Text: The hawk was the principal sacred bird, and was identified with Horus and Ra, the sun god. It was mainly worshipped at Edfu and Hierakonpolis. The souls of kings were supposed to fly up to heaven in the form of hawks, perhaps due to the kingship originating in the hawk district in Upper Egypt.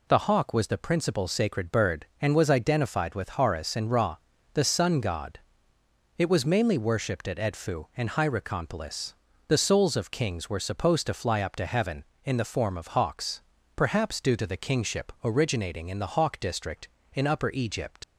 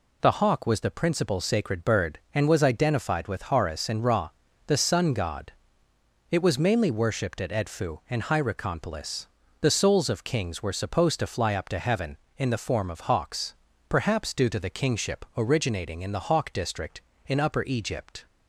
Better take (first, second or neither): second